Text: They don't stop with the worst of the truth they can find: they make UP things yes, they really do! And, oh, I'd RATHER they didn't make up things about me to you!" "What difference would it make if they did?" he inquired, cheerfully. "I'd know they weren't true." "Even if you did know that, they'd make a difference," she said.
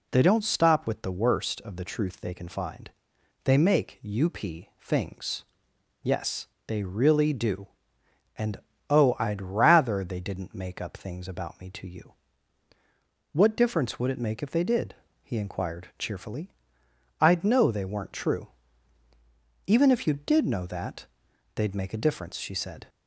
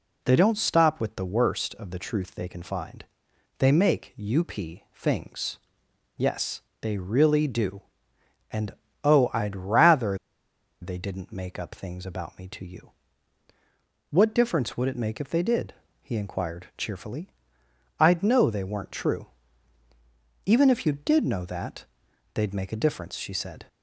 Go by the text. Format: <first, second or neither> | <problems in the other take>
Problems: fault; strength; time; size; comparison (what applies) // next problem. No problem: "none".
first | pauses between "things" and "yes"; noticeable; at 5.5 s; 0.60 s long; noticeable in the first // pauses between "RATHER" and "they"; noticeable; at 10.1 s; 0.63 s long